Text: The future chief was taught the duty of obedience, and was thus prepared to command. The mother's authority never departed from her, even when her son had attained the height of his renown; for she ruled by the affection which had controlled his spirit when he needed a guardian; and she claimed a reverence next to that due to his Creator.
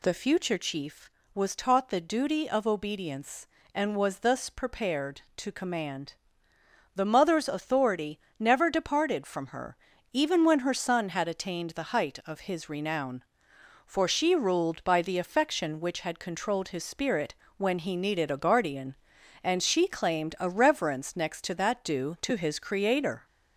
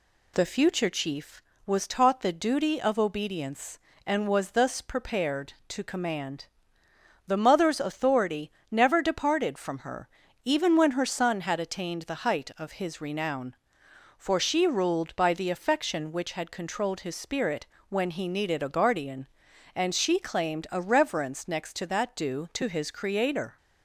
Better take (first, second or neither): second